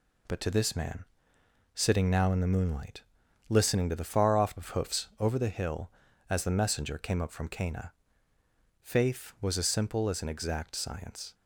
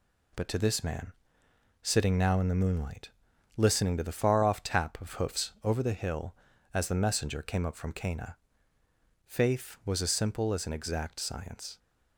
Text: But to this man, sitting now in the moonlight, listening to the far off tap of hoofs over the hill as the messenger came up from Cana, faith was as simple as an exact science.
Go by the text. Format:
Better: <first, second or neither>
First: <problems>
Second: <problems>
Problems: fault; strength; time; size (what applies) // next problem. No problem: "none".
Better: second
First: skips "tap"; at 4.5 s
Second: none